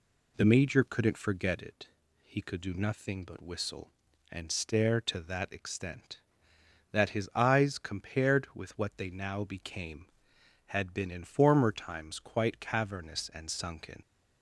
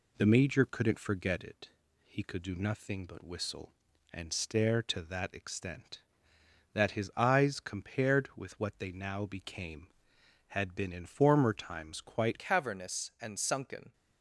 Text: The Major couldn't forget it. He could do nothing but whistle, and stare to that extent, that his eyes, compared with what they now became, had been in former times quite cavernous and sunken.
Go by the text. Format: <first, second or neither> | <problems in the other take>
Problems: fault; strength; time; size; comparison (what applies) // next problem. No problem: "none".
first | changes voice at "cavernous"; from 12.3 s on; 1.6 s long